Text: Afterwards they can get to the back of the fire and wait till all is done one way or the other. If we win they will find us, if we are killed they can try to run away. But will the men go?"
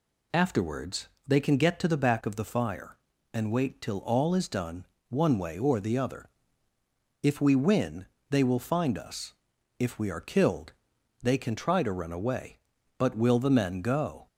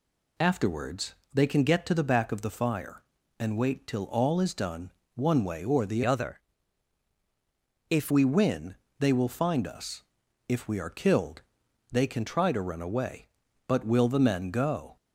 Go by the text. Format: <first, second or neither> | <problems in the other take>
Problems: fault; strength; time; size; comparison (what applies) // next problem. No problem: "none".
first | pauses between "Afterwards" and "they"; slight; at 1.1 s; 0.18 s long; slight in the first // pauses between "done" and "one"; slight; at 4.9 s; 0.24 s long; slight in the first // changes voice from "other" to "If"; from 6.0 to 8.1 s; 2.1 s long // pauses between "win" and "they"; slight; at 8.7 s; 0.24 s long; slight in the first // pauses between "killed" and "they"; noticeable; at 11.4 s; 0.50 s long; noticeable in the first